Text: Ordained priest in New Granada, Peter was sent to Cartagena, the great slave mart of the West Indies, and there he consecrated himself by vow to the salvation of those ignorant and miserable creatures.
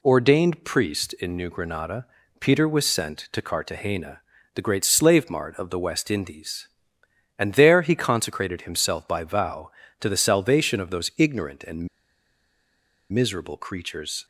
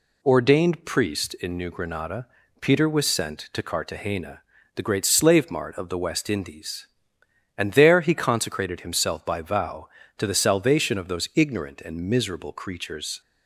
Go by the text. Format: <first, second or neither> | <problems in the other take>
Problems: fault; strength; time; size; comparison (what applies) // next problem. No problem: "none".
second | pauses between "and" and "miserable"; strong; at 11.8 s; 1.2 s long